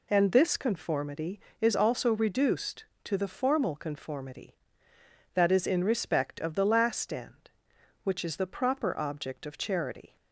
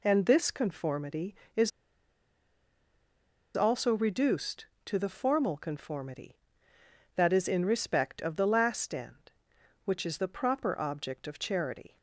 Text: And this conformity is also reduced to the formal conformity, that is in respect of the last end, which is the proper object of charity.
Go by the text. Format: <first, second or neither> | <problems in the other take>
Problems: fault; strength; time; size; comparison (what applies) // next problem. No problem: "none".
first | pauses between "is" and "also"; strong; at 1.7 s; 1.8 s long